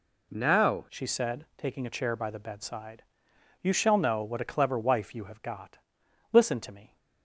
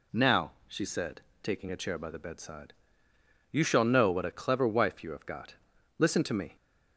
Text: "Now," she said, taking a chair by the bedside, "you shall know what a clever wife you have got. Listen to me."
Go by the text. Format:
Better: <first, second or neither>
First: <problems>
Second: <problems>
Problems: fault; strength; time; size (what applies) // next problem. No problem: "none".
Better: second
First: changes voice at "she"; from 0.8 s on; 6.1 s long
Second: none